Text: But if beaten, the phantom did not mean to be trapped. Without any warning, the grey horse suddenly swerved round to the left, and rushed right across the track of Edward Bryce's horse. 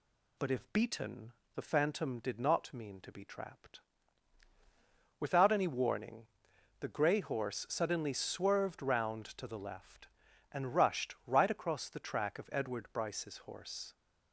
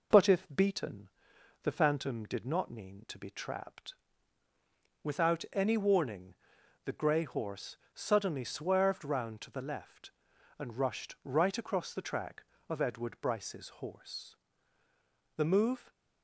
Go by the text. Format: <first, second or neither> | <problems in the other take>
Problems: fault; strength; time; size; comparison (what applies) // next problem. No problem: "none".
first | pauses between "horse" and "suddenly"; slight; at 7.7 s; 0.18 s long // goes on to say "The move"; from 15.3 s on; 0.54 s long